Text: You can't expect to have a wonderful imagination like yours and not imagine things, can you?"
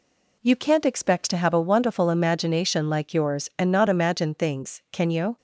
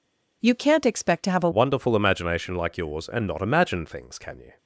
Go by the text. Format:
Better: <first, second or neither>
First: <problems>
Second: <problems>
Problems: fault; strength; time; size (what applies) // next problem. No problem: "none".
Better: first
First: none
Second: changes voice at "wonderful"; from 1.5 s on; 3.0 s long